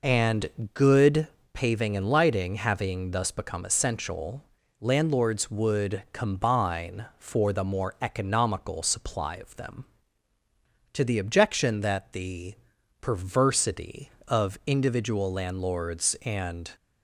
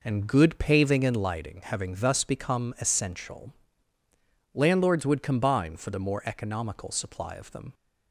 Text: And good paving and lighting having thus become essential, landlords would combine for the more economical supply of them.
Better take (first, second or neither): second